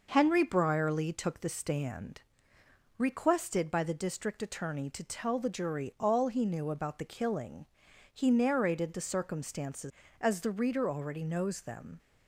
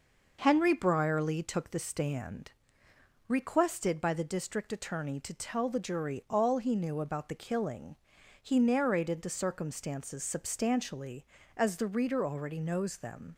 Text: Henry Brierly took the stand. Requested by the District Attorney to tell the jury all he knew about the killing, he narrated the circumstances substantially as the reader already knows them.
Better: second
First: skips "substantially"; at 10.0 s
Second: none

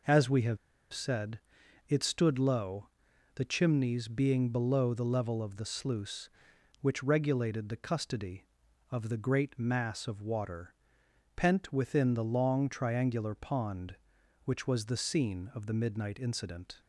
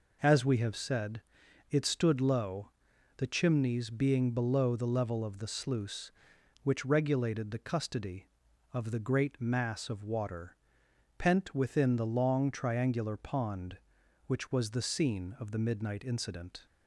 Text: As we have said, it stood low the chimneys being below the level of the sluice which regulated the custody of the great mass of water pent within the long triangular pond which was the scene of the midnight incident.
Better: second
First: pauses between "have" and "said"; slight; at 0.5 s; 0.35 s long // pauses between "low" and "the"; noticeable; at 2.8 s; 0.48 s long // pauses between "water" and "pent"; noticeable; at 10.7 s; 0.64 s long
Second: pauses between "low" and "the"; noticeable; at 2.7 s; 0.48 s long // pauses between "water" and "pent"; noticeable; at 10.5 s; 0.64 s long

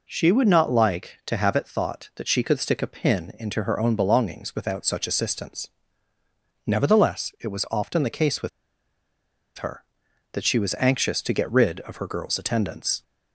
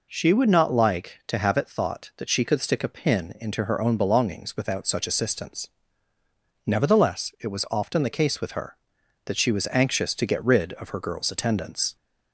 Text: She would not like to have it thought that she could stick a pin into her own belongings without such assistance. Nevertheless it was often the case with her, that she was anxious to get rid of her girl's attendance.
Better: second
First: pauses between "with" and "her"; at 8.4 s; 1.0 s long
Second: none

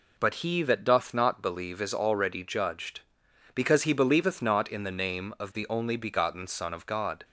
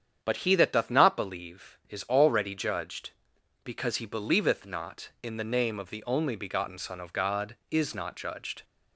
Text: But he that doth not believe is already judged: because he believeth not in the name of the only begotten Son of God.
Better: first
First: none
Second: starts louder than the rest; strong; until 1.2 s; 8.5 dB // goes on to say "Is not judged"; noticeable; from 7.6 s on; 0.94 s long

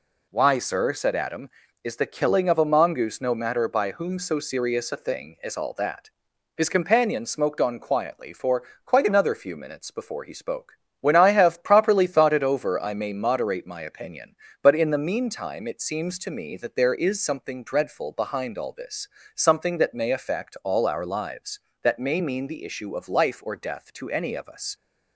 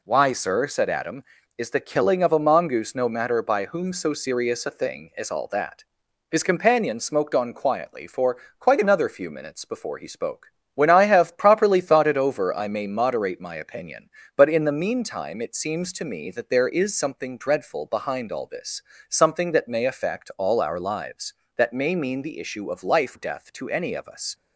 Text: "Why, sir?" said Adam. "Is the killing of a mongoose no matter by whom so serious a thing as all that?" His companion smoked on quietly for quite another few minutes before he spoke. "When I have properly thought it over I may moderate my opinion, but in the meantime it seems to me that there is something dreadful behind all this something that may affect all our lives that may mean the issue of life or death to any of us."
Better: first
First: pauses between "for" and "quite"; slight; at 8.6 s; 0.22 s long // pauses between "this" and "something"; slight; at 19.0 s; 0.26 s long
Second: pauses between "for" and "quite"; slight; at 8.3 s; 0.22 s long // pauses between "this" and "something"; slight; at 18.8 s; 0.26 s long // skips "or"; at 23.1 s

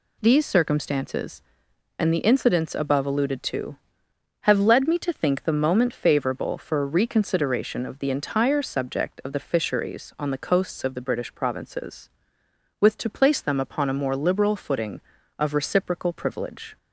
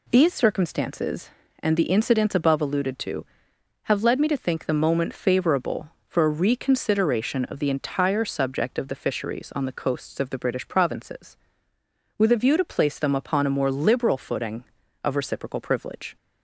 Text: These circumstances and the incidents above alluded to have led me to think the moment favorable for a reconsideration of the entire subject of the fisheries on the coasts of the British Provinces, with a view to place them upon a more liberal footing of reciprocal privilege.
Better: second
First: skips "a view"; at 12.9 s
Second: none

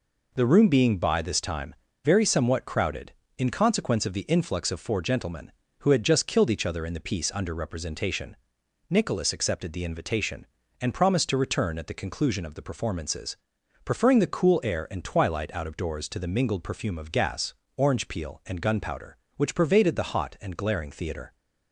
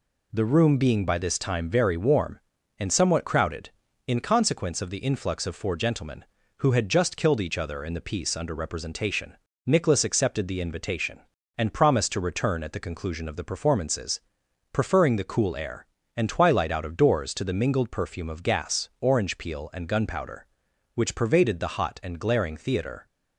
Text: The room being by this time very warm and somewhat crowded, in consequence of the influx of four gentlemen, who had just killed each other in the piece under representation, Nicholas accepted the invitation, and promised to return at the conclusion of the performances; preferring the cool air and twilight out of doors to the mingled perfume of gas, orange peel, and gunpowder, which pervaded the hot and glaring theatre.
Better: second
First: pauses between "time" and "very"; slight; at 1.7 s; 0.30 s long // skips "warm and"; at 2.2 s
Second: none

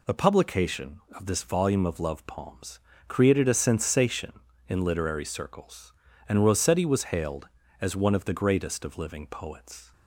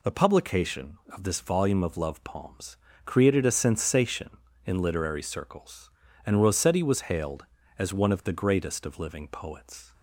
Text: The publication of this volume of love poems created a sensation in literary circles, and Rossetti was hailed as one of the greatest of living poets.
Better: neither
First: pauses between "poems" and "created"; slight; at 2.7 s; 0.26 s long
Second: pauses between "poems" and "created"; slight; at 2.7 s; 0.26 s long

